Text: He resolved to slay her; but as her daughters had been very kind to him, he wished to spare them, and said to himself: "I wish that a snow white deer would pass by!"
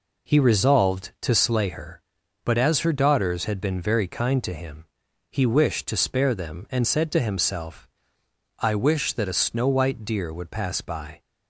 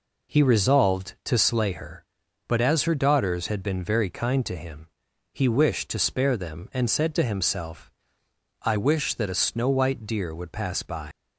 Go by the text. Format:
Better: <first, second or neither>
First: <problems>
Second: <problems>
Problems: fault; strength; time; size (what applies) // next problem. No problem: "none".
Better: first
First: none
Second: leaves "by" unfinished; at 11.1 s; 100 ms